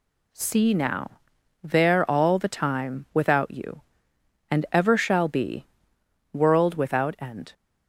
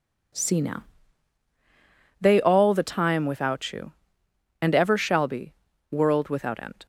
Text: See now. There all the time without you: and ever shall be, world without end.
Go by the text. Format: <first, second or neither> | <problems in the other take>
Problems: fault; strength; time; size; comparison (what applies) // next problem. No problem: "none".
first | says "They" for "There"; at 2.1 s